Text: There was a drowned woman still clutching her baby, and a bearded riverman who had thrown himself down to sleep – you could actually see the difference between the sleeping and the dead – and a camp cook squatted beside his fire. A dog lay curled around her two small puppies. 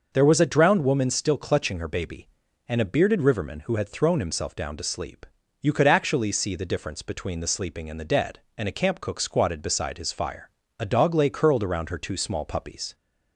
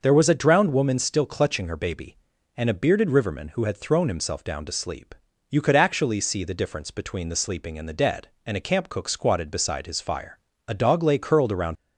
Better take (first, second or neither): first